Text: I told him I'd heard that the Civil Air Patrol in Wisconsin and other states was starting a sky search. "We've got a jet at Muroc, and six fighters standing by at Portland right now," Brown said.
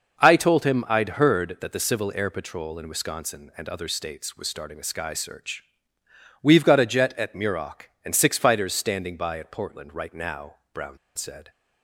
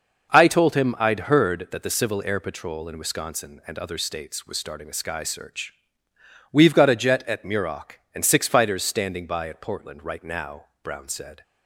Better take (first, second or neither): second